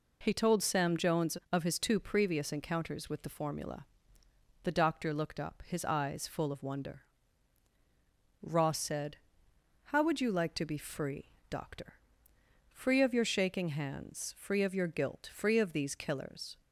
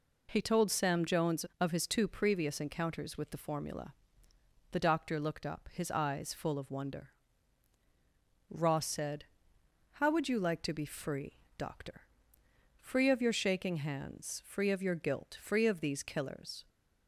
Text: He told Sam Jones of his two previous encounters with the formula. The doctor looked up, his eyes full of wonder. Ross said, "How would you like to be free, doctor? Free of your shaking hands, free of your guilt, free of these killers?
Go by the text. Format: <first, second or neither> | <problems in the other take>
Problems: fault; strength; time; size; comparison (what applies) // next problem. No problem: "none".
neither | none